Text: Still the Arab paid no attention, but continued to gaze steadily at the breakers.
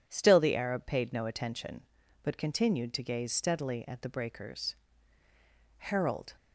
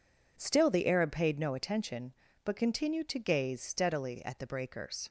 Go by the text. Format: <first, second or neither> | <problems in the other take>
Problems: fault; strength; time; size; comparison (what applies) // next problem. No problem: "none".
second | goes on to say "Harold"; from 5.7 s on; 0.58 s long